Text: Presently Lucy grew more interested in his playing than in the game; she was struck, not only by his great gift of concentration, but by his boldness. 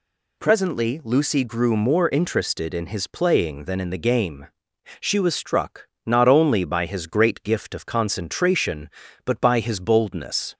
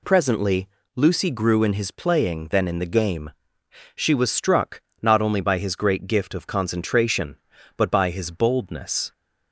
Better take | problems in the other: first | pauses between "Presently" and "Lucy"; slight; at 0.6 s; 0.28 s long // skips "more interested"; at 1.6 s

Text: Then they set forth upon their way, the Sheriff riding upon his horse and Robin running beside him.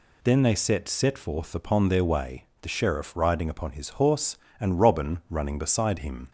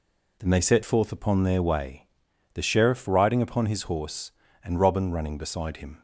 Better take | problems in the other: second | says "set" twice; at 0.8 s

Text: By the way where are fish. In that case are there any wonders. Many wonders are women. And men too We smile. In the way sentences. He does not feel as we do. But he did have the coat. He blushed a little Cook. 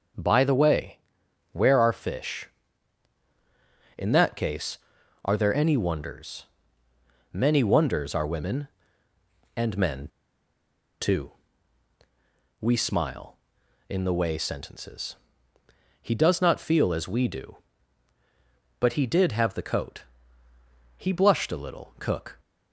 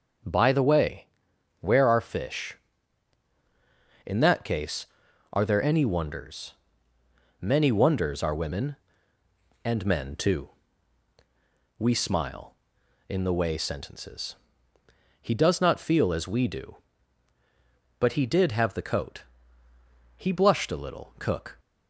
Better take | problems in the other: second | starts louder than the rest; until 1.7 s; 7 dB; also in the second // pauses between "way" and "where"; noticeable; at 0.9 s; 0.54 s long; noticeable in the second // pauses between "men" and "too"; noticeable; at 10.0 s; 0.93 s long // pauses between "too" and "We"; strong; at 11.3 s; 1.2 s long; strong in the second

